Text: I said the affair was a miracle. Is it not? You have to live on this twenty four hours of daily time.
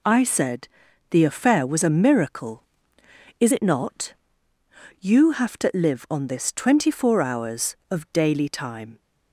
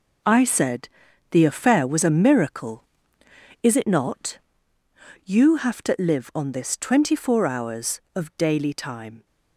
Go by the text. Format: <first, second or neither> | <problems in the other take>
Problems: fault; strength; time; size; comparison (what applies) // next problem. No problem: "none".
first | gets quieter; strong; throughout; 10.5 dB // pauses between "said" and "the"; at 0.8 s; 0.44 s long; also in the first